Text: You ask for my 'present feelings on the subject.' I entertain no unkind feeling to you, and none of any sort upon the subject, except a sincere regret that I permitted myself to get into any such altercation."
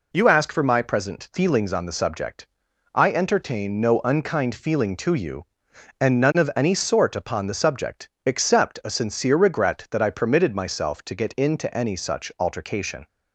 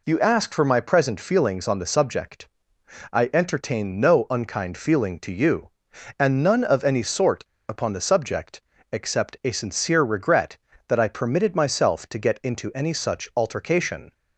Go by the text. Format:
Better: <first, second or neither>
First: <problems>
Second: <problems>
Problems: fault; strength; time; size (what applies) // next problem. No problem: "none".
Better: first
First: none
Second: pauses between "sort" and "upon"; slight; at 7.4 s; 0.22 s long